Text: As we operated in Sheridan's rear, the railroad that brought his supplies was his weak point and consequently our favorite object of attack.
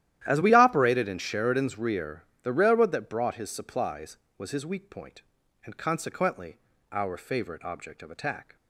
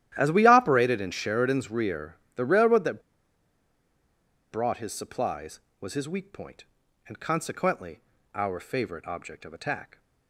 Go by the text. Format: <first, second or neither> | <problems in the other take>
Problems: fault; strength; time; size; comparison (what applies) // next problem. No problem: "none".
first | starts louder than the rest; strong; until 1.1 s; 12.5 dB; strong in the first // pauses between "that" and "brought"; strong; at 3.0 s; 1.5 s long // pauses between "consequently" and "our"; slight; at 8.0 s; 0.34 s long; slight in the first